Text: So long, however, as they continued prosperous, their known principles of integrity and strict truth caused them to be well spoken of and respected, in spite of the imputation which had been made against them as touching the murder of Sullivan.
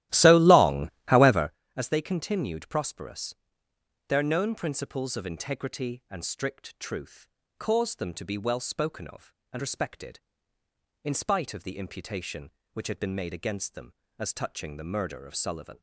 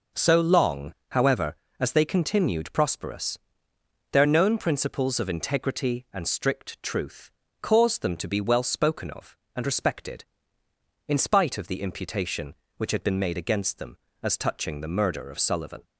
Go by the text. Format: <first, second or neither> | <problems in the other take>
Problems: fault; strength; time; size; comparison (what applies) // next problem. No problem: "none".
second | starts louder than the rest; strong; until 1.7 s; 14.5 dB // pauses between "truth" and "caused"; slight; at 7.2 s; 0.32 s long; slight in the second